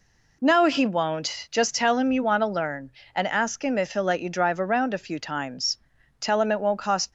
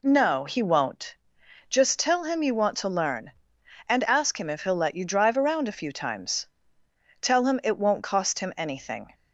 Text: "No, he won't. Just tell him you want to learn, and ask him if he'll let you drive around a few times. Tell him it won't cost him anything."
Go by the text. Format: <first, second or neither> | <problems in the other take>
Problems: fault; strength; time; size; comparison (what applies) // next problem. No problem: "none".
second | stops before "him anything"; at 7.0 s